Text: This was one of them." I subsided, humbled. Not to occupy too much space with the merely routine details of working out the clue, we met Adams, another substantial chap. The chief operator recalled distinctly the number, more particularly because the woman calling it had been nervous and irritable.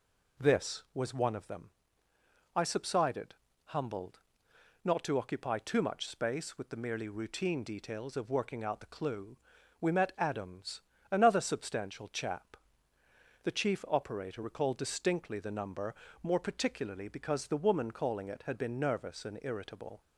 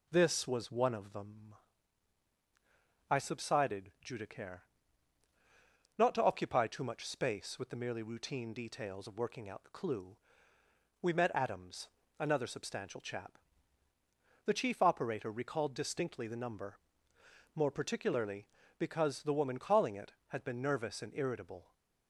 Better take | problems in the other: first | says "judicare" for "humbled"; at 4.0 s

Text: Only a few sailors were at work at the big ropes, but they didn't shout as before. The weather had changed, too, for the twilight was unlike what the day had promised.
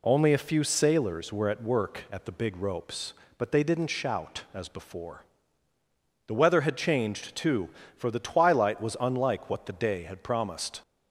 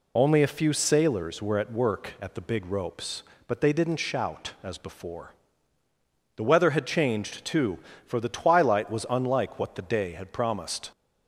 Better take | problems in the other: first | loses the start of "Only"; at 0.1 s; 20 ms

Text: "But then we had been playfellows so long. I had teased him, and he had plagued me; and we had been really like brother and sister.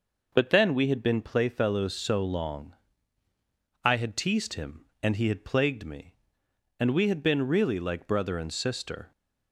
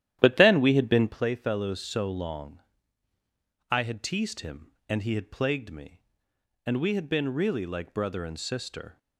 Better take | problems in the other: first | starts louder than the rest; strong; until 1.2 s; 12 dB

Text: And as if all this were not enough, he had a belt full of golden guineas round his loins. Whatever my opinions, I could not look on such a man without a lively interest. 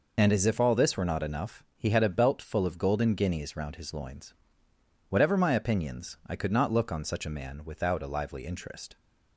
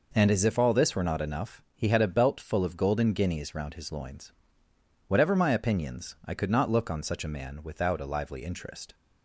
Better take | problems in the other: second | loses the start of "And"; at 0.1 s; 50 ms

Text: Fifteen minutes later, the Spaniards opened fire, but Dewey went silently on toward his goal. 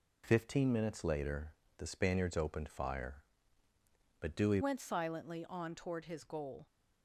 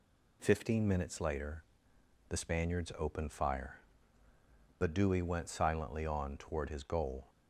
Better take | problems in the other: second | changes voice at "went"; from 4.6 s on; 2.0 s long

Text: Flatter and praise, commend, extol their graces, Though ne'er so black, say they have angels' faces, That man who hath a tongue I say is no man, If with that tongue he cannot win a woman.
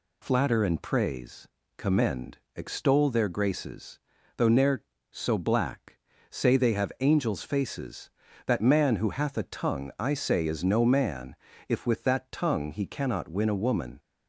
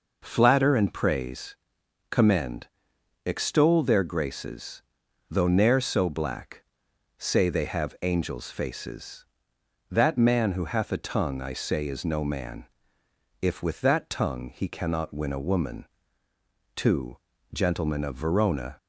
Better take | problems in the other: first | goes on to say "Two Gentlemen of Verona"; strong; from 16.7 s on; 2.0 s long

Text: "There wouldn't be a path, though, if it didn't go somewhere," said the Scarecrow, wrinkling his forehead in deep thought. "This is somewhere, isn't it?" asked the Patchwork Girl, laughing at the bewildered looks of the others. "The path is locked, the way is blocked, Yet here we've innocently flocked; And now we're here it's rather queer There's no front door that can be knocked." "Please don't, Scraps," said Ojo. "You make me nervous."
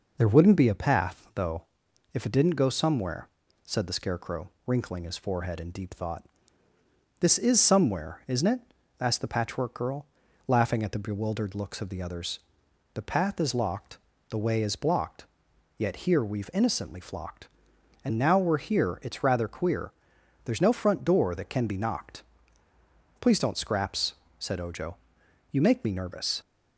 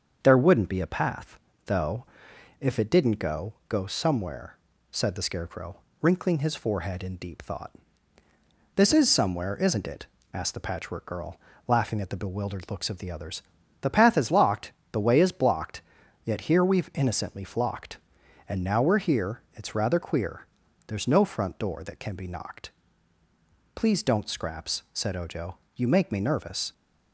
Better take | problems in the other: first | starts louder than the rest; until 1.2 s; 6.5 dB // says "go" twice; at 3.6 s // pauses between "queer" and "There's"; at 20.4 s; 0.42 s long; noticeable in the first

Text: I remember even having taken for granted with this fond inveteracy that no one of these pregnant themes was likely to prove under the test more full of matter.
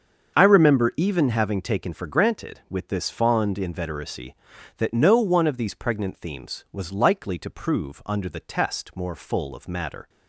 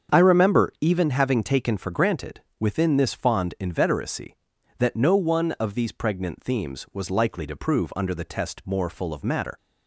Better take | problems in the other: first | starts louder than the rest; strong; until 1.2 s; 7.5 dB; also in the first // says "within" for "with"; at 2.5 s

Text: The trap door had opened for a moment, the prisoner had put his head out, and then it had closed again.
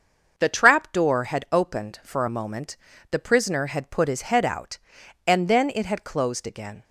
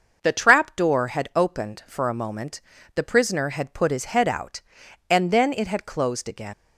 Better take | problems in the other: first | starts louder than the rest; noticeable; until 1.2 s; 6 dB; also in the first // leaves "again" unfinished; at 6.5 s; 115 ms

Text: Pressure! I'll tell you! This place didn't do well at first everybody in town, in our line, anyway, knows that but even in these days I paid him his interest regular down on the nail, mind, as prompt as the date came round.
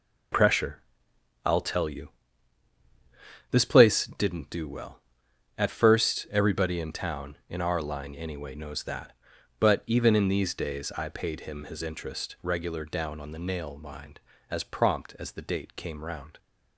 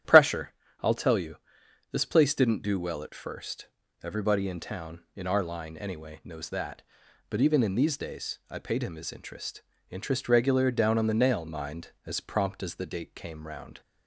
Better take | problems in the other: first | starts louder than the rest; strong; until 1.3 s; 10.5 dB // pauses between "first" and "everybody"; slight; at 3.6 s; 0.34 s long // says "interest" twice; at 9.9 s

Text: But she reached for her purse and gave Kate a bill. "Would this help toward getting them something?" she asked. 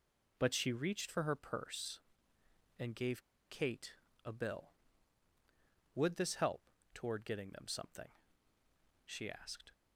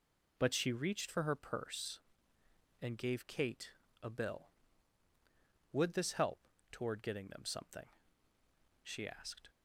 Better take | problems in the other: second | pauses between "gave" and "Kate"; slight; at 3.2 s; 0.27 s long // pauses between "Kate" and "a"; slight; at 3.9 s; 0.30 s long; slight in the second // pauses between "help" and "toward"; slight; at 6.6 s; 0.32 s long; slight in the second

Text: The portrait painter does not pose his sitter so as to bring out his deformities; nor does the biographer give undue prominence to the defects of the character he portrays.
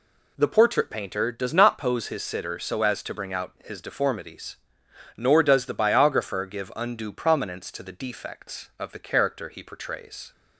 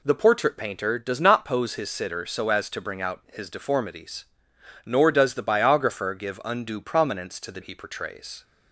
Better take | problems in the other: first | skips "defects of the character"; at 7.6 s

